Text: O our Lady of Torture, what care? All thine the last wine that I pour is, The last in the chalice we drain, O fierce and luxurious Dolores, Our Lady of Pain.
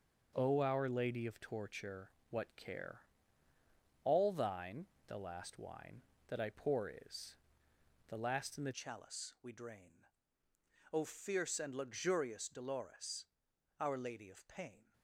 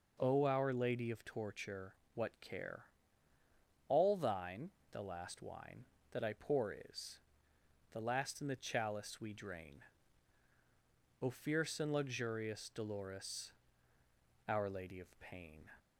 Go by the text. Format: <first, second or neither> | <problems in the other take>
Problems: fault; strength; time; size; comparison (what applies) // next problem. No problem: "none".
second | starts louder than the rest; noticeable; until 1.3 s; 6 dB // pauses between "thine" and "the"; slight; at 4.8 s; 0.20 s long; slight in the second // changes voice at "chalice"; from 8.7 s on; 6.2 s long